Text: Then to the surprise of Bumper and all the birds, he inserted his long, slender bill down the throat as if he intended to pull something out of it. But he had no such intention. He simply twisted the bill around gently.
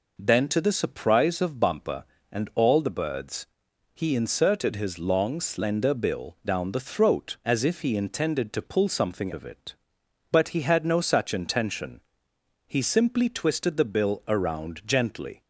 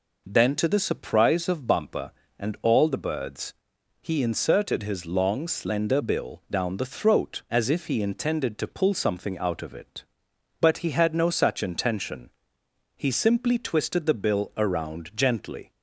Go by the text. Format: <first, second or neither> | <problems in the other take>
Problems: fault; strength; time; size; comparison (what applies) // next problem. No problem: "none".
second | skips "out"; at 9.3 s